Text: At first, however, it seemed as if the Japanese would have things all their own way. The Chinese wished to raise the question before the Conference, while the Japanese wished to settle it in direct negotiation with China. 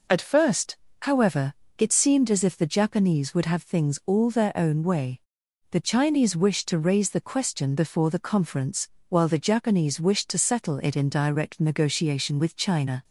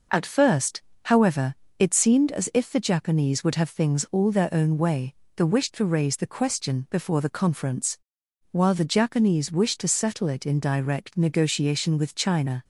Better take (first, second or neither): first